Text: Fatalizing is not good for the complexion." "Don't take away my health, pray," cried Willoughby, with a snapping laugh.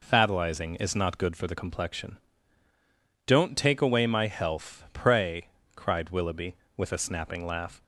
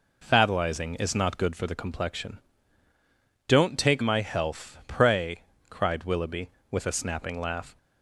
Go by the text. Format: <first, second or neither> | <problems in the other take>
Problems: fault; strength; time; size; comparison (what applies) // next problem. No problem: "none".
first | skips "away"; at 4.0 s